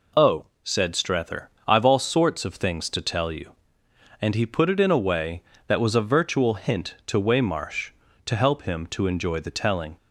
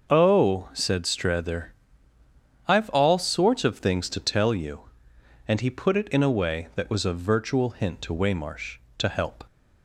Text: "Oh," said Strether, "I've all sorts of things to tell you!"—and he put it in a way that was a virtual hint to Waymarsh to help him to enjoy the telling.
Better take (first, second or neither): first